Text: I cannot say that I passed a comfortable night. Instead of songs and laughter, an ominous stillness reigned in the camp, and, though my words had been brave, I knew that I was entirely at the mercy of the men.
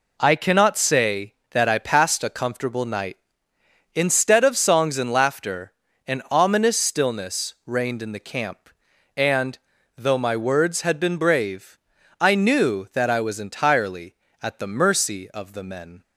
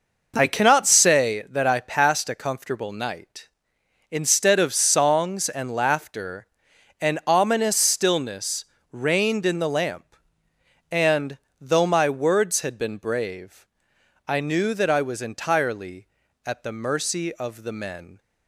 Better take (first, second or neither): first